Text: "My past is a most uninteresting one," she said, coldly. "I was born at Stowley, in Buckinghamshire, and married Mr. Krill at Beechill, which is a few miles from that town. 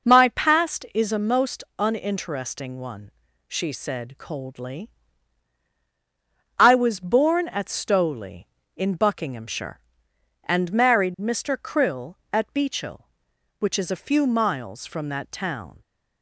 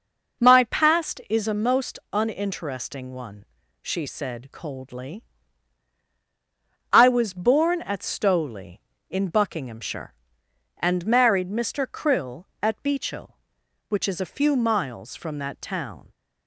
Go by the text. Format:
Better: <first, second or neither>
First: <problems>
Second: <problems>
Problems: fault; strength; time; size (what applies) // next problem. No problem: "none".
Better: neither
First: none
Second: none